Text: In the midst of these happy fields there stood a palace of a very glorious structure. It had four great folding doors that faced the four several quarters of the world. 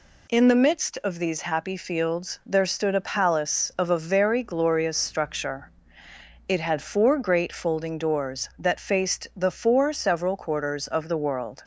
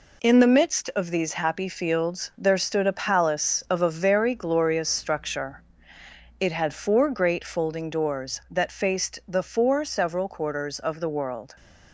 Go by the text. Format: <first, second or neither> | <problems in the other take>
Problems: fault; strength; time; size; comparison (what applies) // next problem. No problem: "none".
first | gets quieter; noticeable; throughout; 6 dB